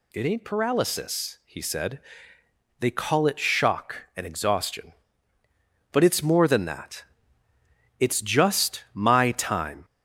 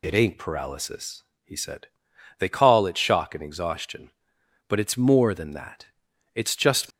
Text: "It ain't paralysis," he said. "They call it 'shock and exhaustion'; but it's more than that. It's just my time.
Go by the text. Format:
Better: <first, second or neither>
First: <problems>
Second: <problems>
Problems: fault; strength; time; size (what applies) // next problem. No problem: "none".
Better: first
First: none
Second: stops before "my time"; at 6.9 s